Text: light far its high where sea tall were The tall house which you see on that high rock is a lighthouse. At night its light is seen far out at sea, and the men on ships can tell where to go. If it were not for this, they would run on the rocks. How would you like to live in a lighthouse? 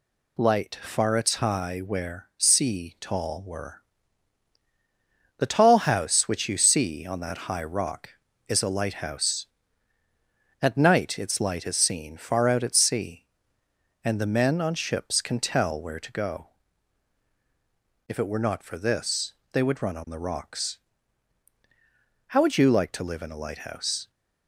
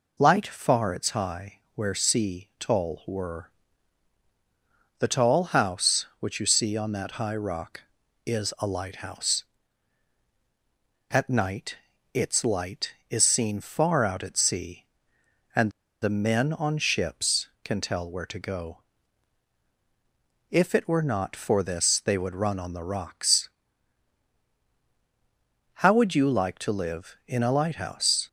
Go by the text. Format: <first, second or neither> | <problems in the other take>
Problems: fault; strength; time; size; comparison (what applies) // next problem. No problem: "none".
first | pauses between "high" and "where"; slight; at 1.5 s; 0.16 s long // pauses between "were" and "The"; strong; at 3.5 s; 1.4 s long; strong in the first // pauses between "night" and "its"; at 11.7 s; 0.38 s long // pauses between "and" and "the"; slight; at 15.6 s; 0.32 s long